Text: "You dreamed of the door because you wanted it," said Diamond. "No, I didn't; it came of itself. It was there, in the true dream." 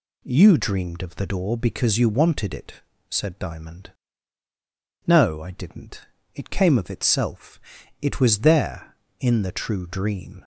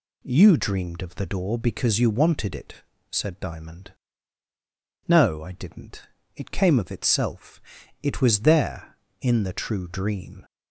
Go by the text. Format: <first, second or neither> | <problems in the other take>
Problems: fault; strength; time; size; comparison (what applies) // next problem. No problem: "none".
neither | none